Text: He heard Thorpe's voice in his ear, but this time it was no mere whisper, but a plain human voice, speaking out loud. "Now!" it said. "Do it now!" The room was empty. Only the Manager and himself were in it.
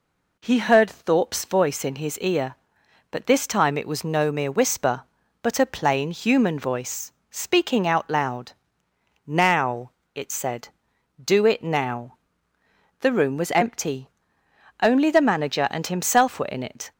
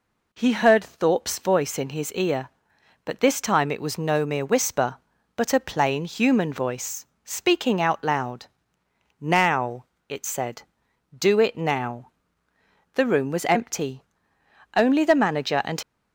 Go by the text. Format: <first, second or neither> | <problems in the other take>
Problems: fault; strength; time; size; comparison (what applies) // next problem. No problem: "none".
first | stops before "himself were in it"; at 15.8 s